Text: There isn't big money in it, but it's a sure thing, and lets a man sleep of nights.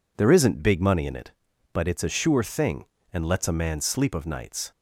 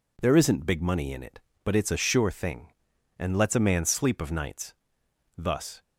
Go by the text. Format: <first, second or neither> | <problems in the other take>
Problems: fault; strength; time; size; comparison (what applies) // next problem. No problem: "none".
first | goes on to say "Thus"; slight; from 5.3 s on; 0.46 s long